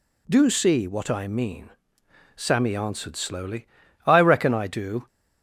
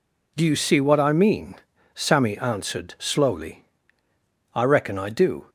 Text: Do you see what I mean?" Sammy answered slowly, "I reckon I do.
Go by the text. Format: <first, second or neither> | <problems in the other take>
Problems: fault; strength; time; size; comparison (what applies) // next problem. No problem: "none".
second | skips "you"; at 0.4 s